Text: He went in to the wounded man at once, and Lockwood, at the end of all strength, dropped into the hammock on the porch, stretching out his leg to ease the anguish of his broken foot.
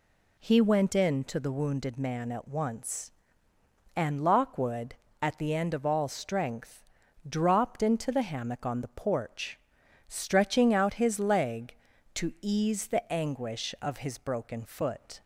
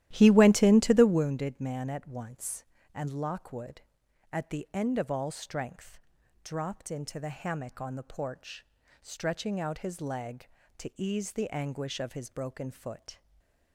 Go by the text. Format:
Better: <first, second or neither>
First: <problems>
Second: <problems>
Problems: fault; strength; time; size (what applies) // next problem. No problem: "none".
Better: first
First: none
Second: starts louder than the rest; strong; until 1.3 s; 13 dB // stays silent after the last word; slight; from 13.1 s on; 0.6 s long